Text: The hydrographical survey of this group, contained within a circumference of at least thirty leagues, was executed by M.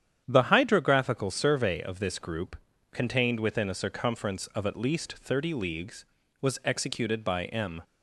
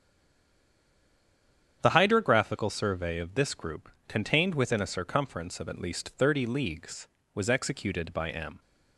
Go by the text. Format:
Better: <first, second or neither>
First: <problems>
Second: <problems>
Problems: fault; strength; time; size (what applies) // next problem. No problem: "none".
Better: first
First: starts louder than the rest; strong; until 1.2 s; 9.5 dB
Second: stays silent before the first word; noticeable; until 1.8 s; 1.8 s long // starts louder than the rest; strong; until 2.8 s; 8.5 dB